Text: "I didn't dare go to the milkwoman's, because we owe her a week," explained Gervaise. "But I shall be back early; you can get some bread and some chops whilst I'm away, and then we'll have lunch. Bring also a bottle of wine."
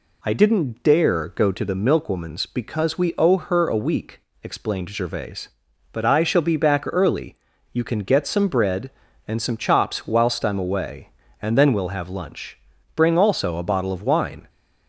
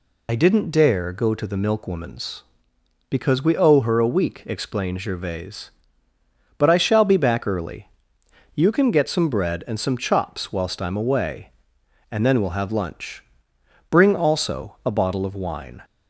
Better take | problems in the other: first | loses the start of "I"; at 0.2 s; 55 ms

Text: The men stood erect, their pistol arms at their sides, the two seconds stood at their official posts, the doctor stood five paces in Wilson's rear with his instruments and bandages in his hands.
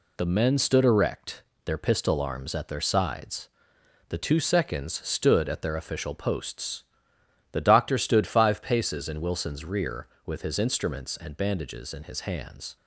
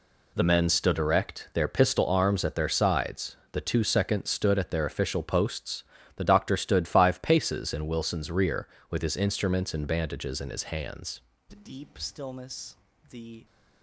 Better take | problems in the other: first | goes on to say "The deep stillness the"; strong; from 11.4 s on; 1.9 s long

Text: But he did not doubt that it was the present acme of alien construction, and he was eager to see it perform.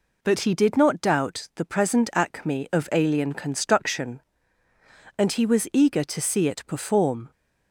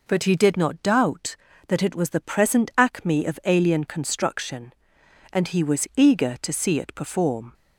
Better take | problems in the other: second | skips "that it was"; at 1.5 s

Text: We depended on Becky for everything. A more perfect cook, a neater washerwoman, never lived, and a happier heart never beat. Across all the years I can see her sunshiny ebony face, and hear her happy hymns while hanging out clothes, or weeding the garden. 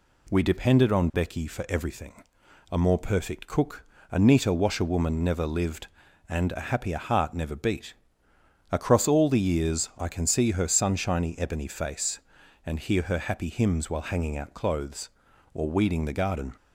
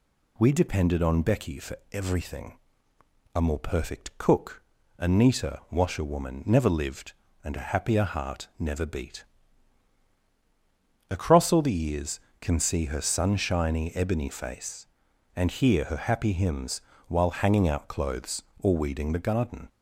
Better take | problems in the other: first | pauses between "for" and "everything"; slight; at 1.7 s; 0.16 s long // skips "I"; at 12.2 s // pauses between "hymns" and "while"; slight; at 16.8 s; 0.24 s long

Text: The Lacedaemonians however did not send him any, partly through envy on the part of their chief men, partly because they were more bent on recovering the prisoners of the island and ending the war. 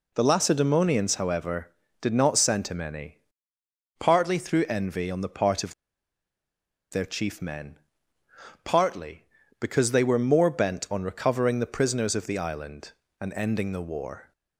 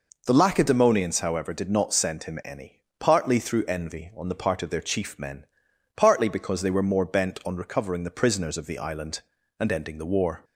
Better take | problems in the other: second | pauses between "of" and "their"; at 5.7 s; 1.1 s long

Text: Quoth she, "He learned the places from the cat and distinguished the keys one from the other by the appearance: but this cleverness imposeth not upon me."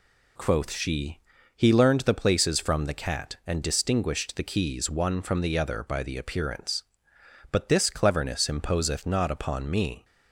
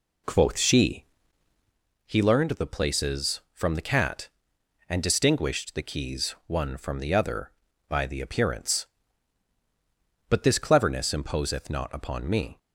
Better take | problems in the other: first | starts louder than the rest; slight; until 1.8 s; 3 dB

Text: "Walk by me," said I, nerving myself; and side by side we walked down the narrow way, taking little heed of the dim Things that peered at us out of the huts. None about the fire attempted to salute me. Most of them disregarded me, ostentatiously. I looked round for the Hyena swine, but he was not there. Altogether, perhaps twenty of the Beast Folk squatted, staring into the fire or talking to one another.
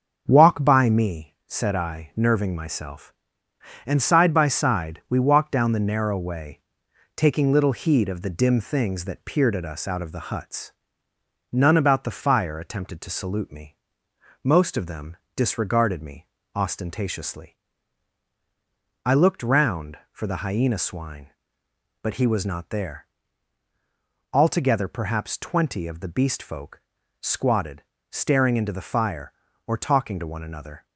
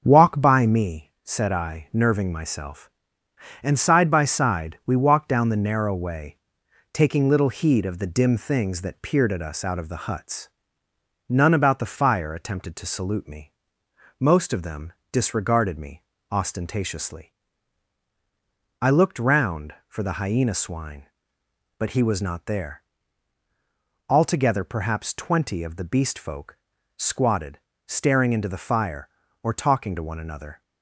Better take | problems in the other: neither | starts louder than the rest; the same in both // pauses between "them" and "disregarded"; slight; the same in both // pauses between "Folk" and "squatted"; the same in both

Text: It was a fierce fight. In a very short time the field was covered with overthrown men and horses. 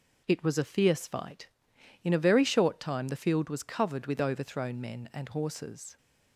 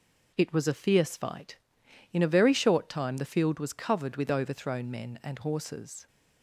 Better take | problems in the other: neither | none

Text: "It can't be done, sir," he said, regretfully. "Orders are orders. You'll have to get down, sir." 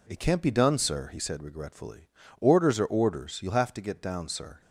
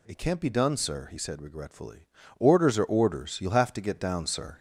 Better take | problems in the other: first | gets louder; noticeable; throughout; 4 dB

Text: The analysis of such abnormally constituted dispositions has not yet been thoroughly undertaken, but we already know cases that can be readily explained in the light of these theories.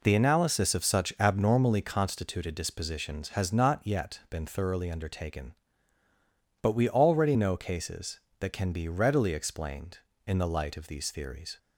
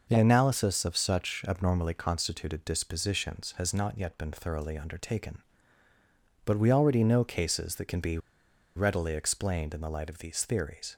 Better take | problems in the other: first | pauses between "be" and "readily"; noticeable; at 8.1 s; 0.58 s long

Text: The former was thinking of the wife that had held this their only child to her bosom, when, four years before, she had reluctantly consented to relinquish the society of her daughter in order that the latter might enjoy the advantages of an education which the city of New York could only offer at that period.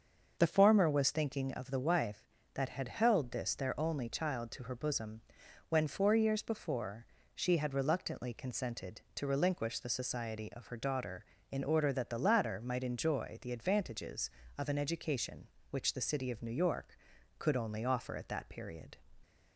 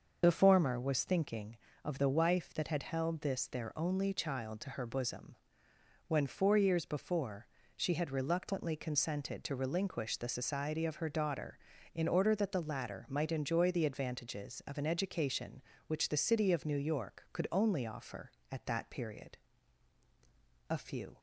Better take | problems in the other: first | starts louder than the rest; noticeable; until 1.2 s; 6 dB; also in the first // goes on to say "A few"; slight; from 20.7 s on; 0.48 s long

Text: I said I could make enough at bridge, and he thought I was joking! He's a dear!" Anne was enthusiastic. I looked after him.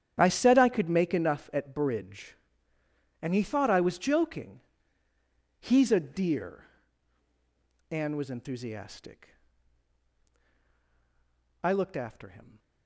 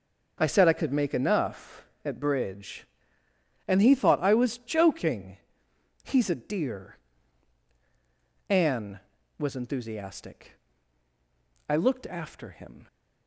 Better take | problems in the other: second | gets quieter; strong; throughout; 16 dB // starts louder than the rest; strong; until 1.1 s; 9.5 dB; also in the second

